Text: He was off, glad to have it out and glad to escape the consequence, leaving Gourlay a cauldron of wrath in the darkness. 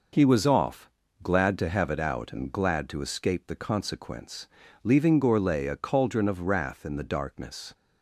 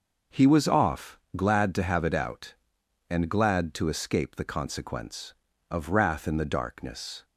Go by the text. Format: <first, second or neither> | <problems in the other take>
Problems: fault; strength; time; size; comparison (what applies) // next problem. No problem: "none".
first | starts louder than the rest; noticeable; until 1.4 s; 6 dB // skips "leaving Gourlay a cauldron"; at 5.5 s